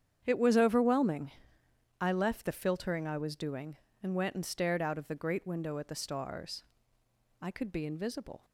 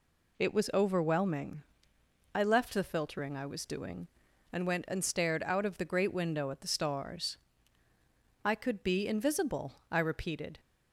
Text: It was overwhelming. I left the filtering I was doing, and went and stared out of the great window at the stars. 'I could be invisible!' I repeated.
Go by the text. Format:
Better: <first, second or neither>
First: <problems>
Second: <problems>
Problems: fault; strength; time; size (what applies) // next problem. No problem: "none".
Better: second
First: starts louder than the rest; strong; until 1.2 s; 8.5 dB // stops before "I repeated"; at 8.4 s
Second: none